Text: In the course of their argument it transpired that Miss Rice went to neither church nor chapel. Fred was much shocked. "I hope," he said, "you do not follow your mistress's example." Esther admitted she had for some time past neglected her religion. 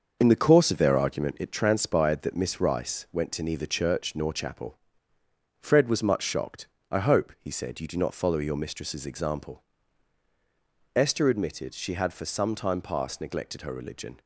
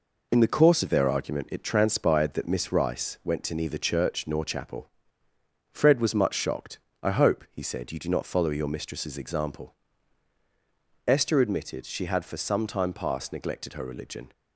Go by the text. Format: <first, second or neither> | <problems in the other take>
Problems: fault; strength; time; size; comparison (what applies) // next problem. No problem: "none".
second | starts louder than the rest; until 1.6 s; 6.5 dB